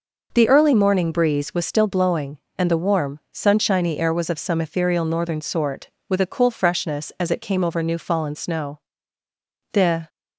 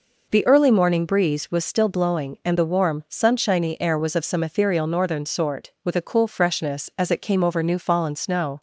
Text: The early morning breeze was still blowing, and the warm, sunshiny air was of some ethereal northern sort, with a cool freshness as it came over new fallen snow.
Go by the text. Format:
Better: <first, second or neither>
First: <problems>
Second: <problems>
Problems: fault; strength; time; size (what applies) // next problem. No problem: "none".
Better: second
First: goes on to say "The"; slight; from 9.7 s on; 0.36 s long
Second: none